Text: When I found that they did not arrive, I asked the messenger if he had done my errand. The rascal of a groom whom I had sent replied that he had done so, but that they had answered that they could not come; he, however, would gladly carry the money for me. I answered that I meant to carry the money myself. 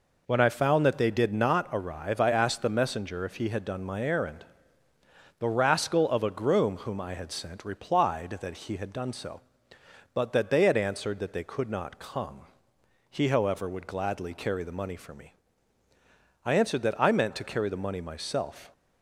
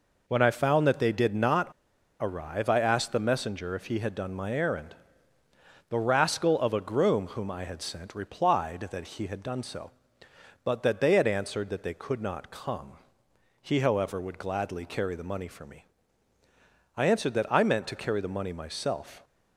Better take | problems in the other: first | pauses between "not" and "arrive"; noticeable; at 1.7 s; 0.49 s long

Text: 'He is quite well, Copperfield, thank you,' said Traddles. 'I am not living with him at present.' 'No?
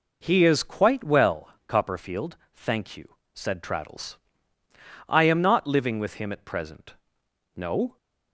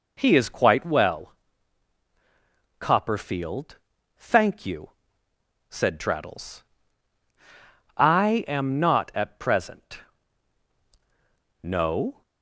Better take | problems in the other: first | skips "living with him"; at 9.1 s

